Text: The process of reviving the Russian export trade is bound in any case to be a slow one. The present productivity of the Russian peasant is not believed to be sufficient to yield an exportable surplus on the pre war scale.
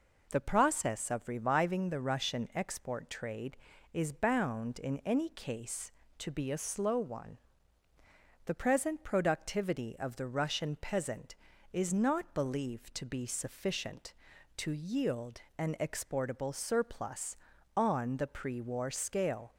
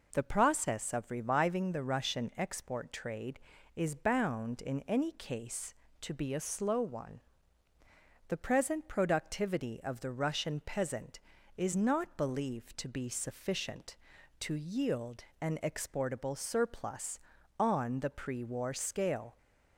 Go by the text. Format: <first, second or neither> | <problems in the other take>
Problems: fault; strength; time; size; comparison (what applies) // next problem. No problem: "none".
neither | pauses between "yield" and "an"; slight; the same in both